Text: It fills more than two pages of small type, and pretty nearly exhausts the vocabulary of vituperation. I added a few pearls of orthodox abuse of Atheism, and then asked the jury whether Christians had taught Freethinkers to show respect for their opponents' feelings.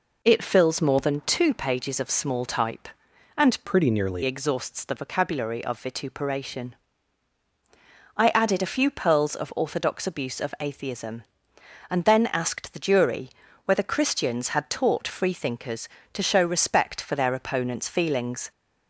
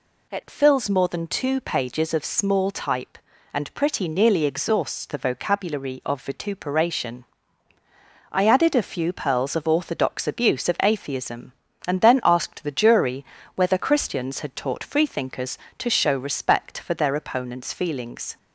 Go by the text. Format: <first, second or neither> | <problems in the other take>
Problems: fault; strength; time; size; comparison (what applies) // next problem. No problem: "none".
second | changes voice from "pretty" to "nearly"; from 3.6 to 4.2 s; 0.6 s long // pauses between "jury" and "whether"; slight; at 13.2 s; 0.36 s long; slight in the second